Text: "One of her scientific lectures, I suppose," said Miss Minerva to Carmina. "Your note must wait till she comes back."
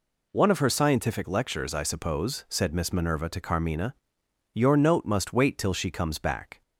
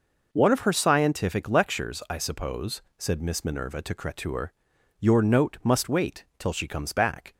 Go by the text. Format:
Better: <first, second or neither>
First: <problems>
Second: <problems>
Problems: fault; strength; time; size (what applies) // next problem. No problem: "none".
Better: first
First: none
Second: says "Cretur" for "Carmina"; at 3.9 s